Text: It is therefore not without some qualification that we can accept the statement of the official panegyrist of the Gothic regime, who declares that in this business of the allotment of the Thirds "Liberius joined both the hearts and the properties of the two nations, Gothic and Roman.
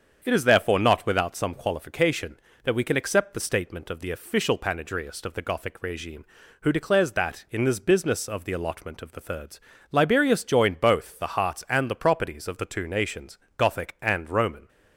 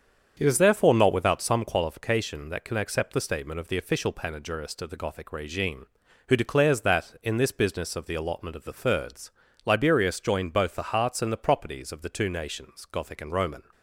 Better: first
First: starts louder than the rest; strong; until 1.2 s; 7.5 dB // pauses between "Thirds" and "Liberius"; slight; at 9.5 s; 0.30 s long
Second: starts louder than the rest; strong; until 1.3 s; 7.5 dB // skips "we"; at 2.6 s // pauses between "Thirds" and "Liberius"; slight; at 9.3 s; 0.34 s long

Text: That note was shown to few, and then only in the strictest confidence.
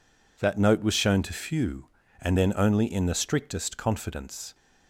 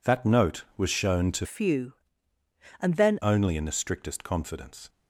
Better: first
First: none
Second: changes voice from "few" to "then"; from 1.4 to 3.1 s; 1.7 s long

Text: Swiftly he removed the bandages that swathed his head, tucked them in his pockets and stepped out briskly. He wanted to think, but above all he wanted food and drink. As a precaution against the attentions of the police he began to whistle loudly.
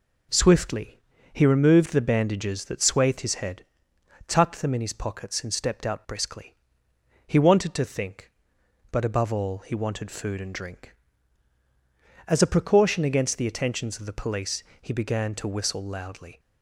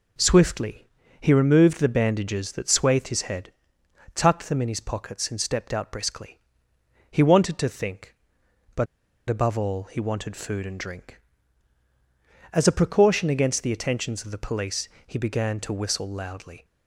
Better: first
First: pauses between "Swiftly" and "he"; slight; at 0.9 s; 0.34 s long // pauses between "police" and "he"; slight; at 14.6 s; 0.18 s long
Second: pauses between "Swiftly" and "he"; slight; at 0.8 s; 0.34 s long // pauses between "but" and "above"; at 8.8 s; 0.44 s long // pauses between "police" and "he"; slight; at 14.8 s; 0.18 s long

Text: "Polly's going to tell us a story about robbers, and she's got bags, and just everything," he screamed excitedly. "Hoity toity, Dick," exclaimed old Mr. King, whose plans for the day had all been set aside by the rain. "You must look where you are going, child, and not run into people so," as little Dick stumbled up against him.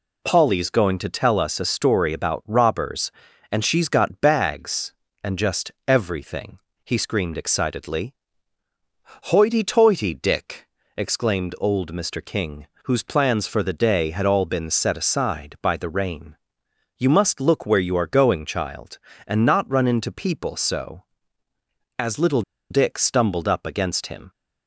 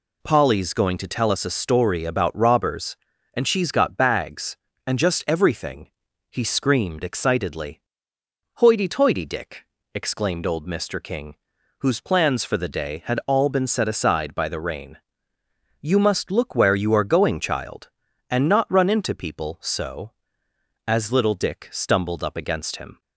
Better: second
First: pauses between "just" and "everything"; slight; at 5.7 s; 0.16 s long // pauses between "little" and "Dick"; slight; at 22.4 s; 0.28 s long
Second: none

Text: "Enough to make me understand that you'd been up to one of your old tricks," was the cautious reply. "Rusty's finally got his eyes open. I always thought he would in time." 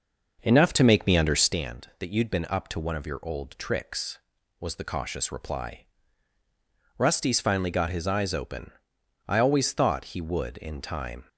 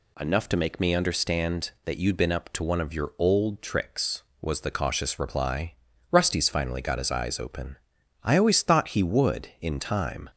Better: second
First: starts louder than the rest; noticeable; until 1.6 s; 6 dB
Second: none

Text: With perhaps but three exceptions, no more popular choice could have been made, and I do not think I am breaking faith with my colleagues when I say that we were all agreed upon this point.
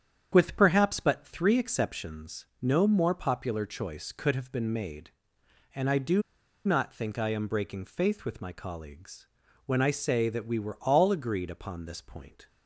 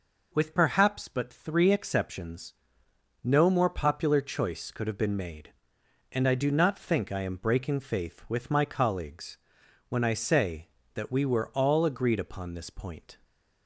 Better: second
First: starts louder than the rest; strong; until 1.3 s; 8 dB // pauses between "do" and "not"; at 6.2 s; 0.44 s long // pauses between "colleagues" and "when"; at 9.2 s; 0.40 s long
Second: pauses between "colleagues" and "when"; noticeable; at 9.3 s; 0.50 s long

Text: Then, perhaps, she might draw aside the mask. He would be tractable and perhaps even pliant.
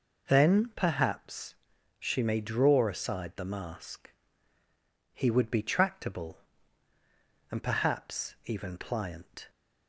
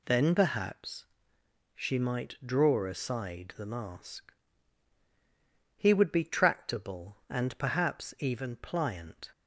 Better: second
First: says "may" for "might"; at 2.2 s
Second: none

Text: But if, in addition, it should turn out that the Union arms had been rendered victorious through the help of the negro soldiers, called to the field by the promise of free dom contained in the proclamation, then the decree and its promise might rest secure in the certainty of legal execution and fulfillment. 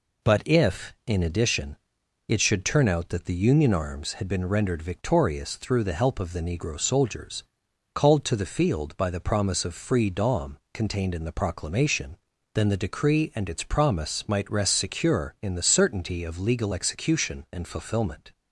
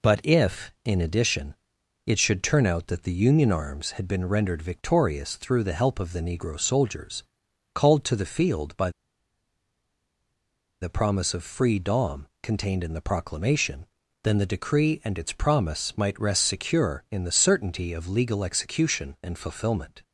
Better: first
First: pauses between "dom" and "contained"; slight; at 10.5 s; 0.16 s long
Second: pauses between "by" and "the"; strong; at 8.8 s; 1.9 s long // pauses between "dom" and "contained"; slight; at 12.2 s; 0.16 s long

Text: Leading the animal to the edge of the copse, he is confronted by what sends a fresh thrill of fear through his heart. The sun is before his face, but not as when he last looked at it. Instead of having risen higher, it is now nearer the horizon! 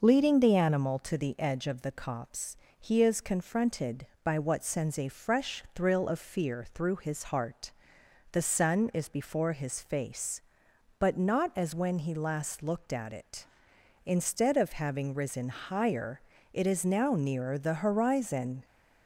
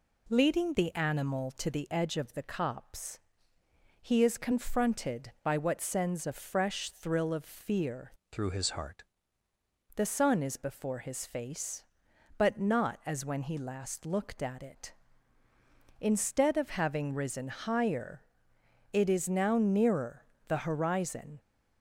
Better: first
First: none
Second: changes voice from "through" to "heart"; from 8.3 to 9.0 s; 0.7 s long // pauses between "nearer" and "the"; slight; at 20.2 s; 0.22 s long

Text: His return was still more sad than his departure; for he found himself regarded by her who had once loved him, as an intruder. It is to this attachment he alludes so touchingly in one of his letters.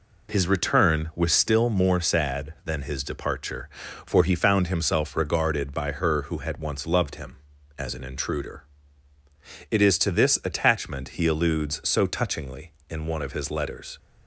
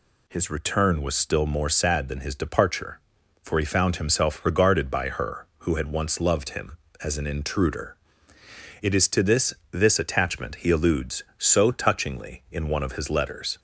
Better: first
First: none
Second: says "this" twice; at 9.7 s

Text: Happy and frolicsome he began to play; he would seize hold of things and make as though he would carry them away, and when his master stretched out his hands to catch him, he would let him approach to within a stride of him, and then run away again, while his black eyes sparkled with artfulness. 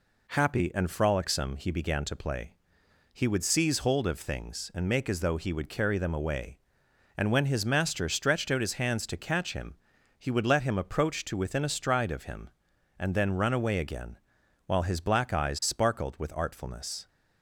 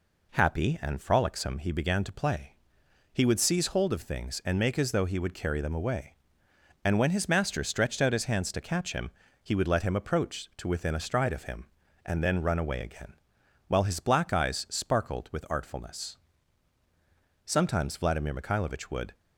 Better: first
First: none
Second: goes on to say "Sometimes Vladimir Mikhailovich would"; strong; from 17.4 s on; 1.7 s long

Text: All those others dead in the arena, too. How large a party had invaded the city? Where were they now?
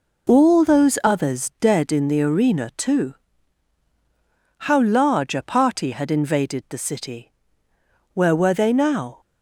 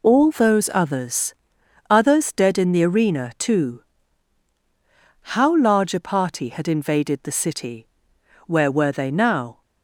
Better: first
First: none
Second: says "others" twice; at 1.8 s

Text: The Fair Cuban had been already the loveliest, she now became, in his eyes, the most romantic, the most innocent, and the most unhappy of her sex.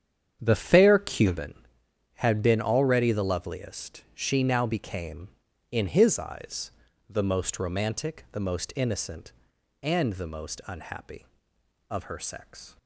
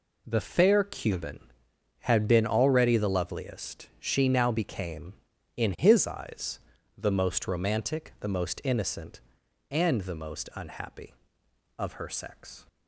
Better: second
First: starts louder than the rest; strong; until 1.5 s; 8.5 dB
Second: none

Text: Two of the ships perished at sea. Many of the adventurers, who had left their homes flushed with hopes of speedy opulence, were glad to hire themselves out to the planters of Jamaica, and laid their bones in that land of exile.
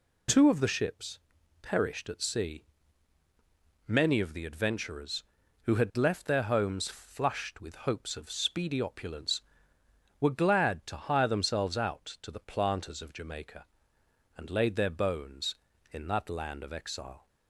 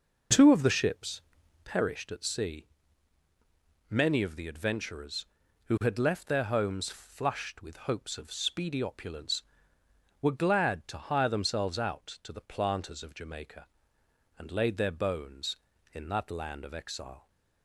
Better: first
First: pauses between "ships" and "perished"; noticeable; at 1.1 s; 0.46 s long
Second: starts louder than the rest; noticeable; until 1.8 s; 5.5 dB // pauses between "ships" and "perished"; noticeable; at 1.1 s; 0.46 s long

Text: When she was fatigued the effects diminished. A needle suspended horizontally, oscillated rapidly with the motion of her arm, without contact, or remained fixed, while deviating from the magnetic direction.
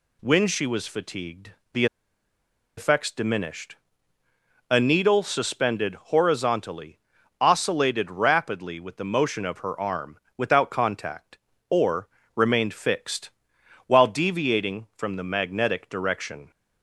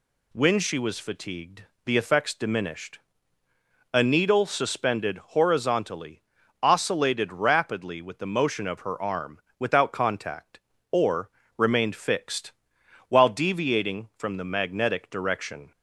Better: second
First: pauses between "fatigued" and "the"; slight; at 1.5 s; 0.20 s long // pauses between "the" and "effects"; noticeable; at 1.8 s; 0.91 s long // pauses between "or" and "remained"; slight; at 12.0 s; 0.26 s long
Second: pauses between "fatigued" and "the"; slight; at 1.6 s; 0.20 s long // pauses between "or" and "remained"; slight; at 11.3 s; 0.26 s long

